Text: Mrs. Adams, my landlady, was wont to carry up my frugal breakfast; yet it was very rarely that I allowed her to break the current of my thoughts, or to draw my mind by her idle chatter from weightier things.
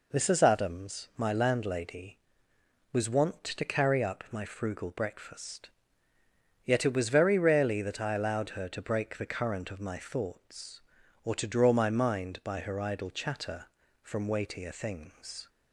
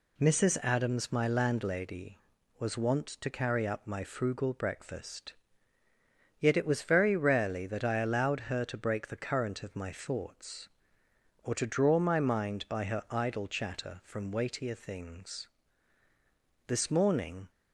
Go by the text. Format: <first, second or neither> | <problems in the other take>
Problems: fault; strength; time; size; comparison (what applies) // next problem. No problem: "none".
first | goes on to say "This morning"; noticeable; from 16.6 s on; 0.82 s long